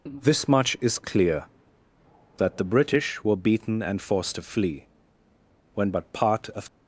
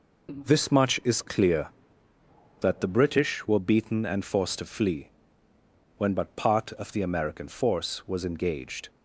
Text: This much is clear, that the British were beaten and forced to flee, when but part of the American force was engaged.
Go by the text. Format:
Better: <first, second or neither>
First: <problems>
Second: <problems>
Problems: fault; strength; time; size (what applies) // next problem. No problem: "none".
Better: second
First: stops before "the American force was engaged"; at 6.6 s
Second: none